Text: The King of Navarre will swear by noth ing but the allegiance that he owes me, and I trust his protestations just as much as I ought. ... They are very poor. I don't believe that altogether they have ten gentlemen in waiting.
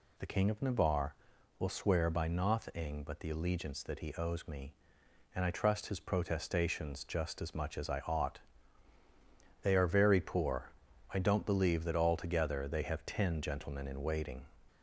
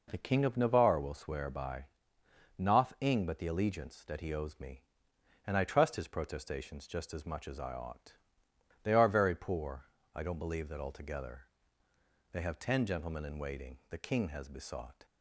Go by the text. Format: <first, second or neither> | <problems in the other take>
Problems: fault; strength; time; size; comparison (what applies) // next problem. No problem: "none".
first | pauses between "by" and "noth"; noticeable; at 1.8 s; 0.72 s long // pauses between "altogether" and "they"; noticeable; at 11.4 s; 0.88 s long // goes on to say "The King has besought"; noticeable; from 13.9 s on; 1.1 s long